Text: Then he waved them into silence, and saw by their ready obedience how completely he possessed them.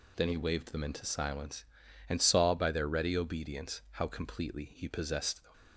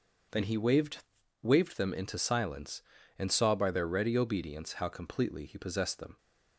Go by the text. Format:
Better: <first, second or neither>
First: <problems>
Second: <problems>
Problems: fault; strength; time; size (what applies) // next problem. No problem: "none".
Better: first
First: none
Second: says "waved" twice; at 1.4 s